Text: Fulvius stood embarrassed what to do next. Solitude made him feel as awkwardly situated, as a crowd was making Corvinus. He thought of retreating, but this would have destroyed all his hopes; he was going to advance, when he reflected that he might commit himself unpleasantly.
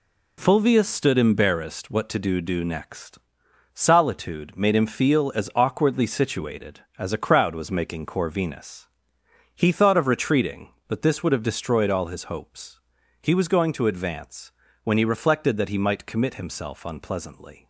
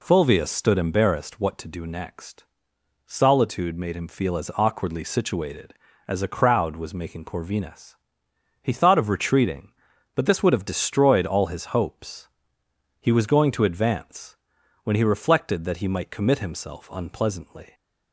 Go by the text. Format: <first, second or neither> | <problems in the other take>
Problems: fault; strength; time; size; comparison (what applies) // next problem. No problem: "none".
second | says "do" twice; at 2.3 s